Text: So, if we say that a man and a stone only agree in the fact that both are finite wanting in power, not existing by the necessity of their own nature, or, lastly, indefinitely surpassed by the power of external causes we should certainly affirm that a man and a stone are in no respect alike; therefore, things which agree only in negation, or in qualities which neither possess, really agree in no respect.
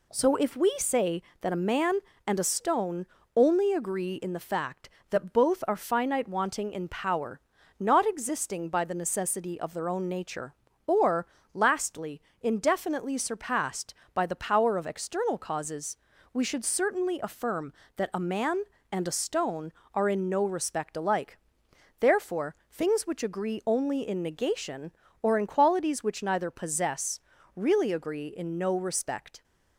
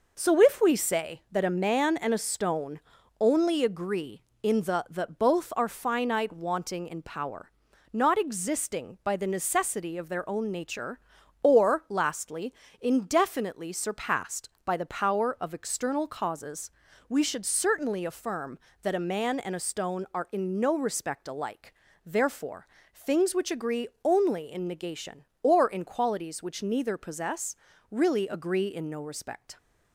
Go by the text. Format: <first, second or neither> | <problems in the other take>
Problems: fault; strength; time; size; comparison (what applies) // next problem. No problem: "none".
first | pauses between "stone" and "only"; at 2.7 s; 0.40 s long; slight in the first // skips "fact"; at 4.8 s // pauses between "causes" and "we"; at 16.7 s; 0.38 s long; slight in the first // pauses between "agree" and "only"; slight; at 23.8 s; 0.16 s long